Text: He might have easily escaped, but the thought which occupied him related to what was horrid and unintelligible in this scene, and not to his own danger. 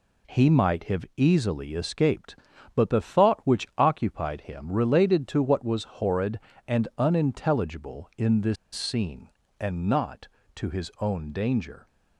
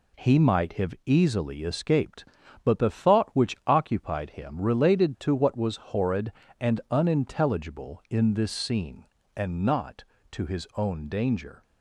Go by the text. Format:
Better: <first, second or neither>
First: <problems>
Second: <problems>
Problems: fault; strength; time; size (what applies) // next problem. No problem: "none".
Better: second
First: pauses between "this" and "scene"; slight; at 8.5 s; 0.18 s long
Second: none